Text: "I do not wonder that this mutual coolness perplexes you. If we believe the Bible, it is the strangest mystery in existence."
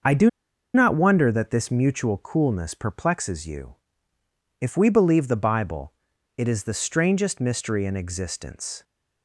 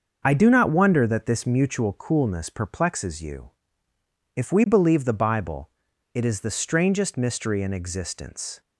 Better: second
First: starts louder than the rest; until 1.5 s; 6.5 dB // pauses between "do" and "not"; at 0.2 s; 0.45 s long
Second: starts louder than the rest; until 1.2 s; 6.5 dB

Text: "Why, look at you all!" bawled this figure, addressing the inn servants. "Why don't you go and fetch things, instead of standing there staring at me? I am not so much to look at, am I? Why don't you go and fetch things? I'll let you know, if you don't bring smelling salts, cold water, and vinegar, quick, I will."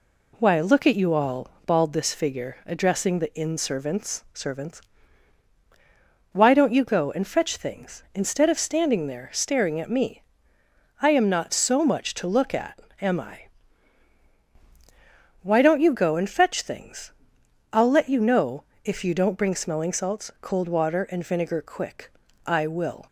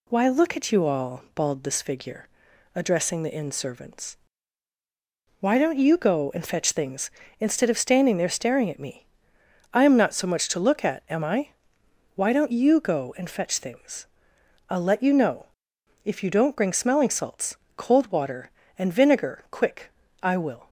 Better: second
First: says "servants" twice; at 4.3 s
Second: none

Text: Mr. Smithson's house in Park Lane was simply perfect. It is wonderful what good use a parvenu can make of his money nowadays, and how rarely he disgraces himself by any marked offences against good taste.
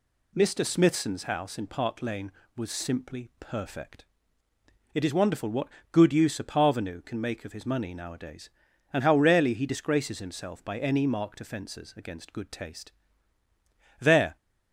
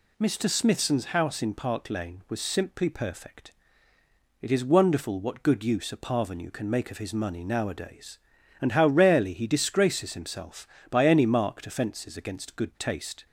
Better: second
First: pauses between "what" and "good"; slight; at 5.6 s; 0.24 s long // goes on to say "There"; slight; from 13.9 s on; 0.36 s long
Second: none

